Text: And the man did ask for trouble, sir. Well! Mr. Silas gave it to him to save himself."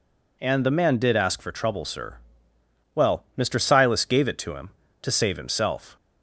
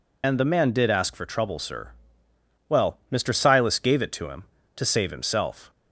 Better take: first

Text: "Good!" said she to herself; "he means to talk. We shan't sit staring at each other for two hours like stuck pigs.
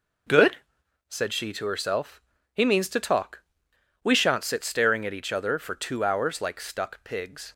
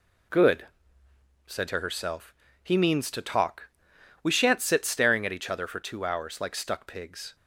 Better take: first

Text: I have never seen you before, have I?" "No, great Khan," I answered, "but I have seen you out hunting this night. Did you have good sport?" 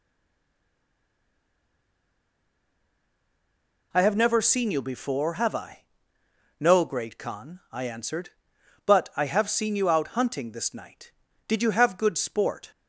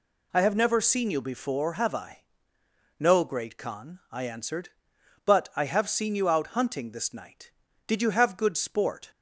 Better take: second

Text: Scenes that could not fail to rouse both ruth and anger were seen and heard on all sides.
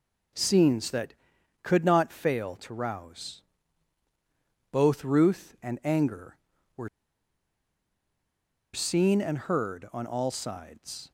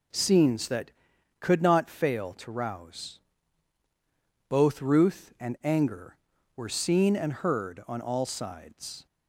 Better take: second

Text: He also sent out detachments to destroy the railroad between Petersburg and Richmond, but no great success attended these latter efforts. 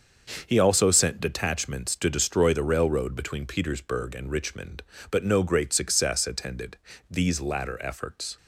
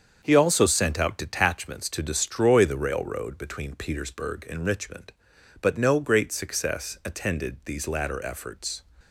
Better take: second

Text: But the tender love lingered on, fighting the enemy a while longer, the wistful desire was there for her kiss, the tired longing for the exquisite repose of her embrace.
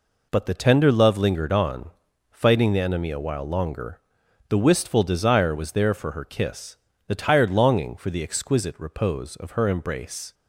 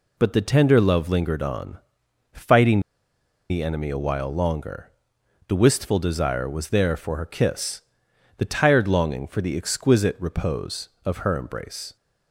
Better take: first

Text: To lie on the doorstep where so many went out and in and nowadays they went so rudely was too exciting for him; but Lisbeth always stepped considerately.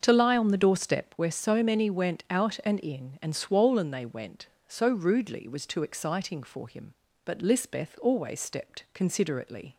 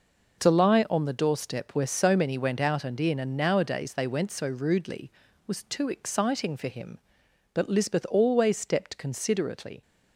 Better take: second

